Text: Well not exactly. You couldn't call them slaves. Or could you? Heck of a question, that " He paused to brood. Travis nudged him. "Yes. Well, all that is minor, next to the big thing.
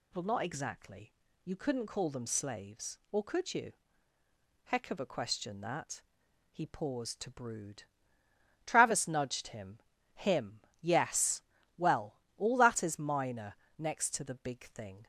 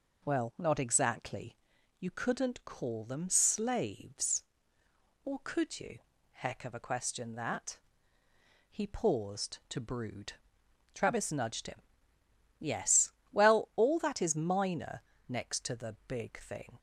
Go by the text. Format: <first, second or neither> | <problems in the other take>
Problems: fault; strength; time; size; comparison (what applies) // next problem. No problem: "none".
second | says "him" twice; at 10.1 s